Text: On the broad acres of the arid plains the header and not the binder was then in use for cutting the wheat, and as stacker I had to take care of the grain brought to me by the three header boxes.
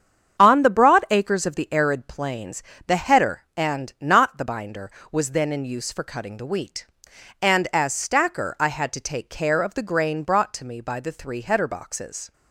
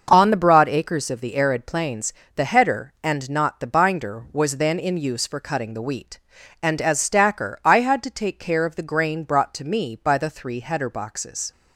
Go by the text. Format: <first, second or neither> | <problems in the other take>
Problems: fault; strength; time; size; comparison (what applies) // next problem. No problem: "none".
neither | starts louder than the rest; the same in both // pauses between "plains" and "the"; slight; the same in both